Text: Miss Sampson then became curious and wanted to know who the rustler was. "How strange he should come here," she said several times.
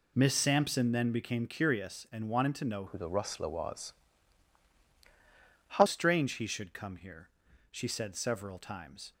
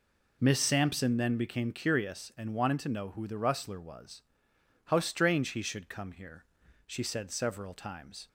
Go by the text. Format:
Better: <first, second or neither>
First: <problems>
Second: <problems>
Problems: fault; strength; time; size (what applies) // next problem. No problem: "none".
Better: second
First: changes voice from "who" to "How"; from 2.8 to 5.8 s; 3.0 s long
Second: none